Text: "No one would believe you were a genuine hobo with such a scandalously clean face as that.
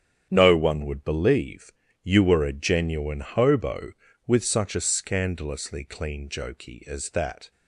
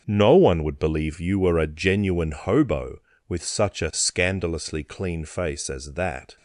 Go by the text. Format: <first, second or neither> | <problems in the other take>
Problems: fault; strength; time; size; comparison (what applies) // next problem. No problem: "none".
second | starts louder than the rest; strong; until 1.3 s; 9 dB; also in the second // pauses between "believe" and "you"; slight; at 1.7 s; 0.32 s long // says "jokey" for "face"; at 6.3 s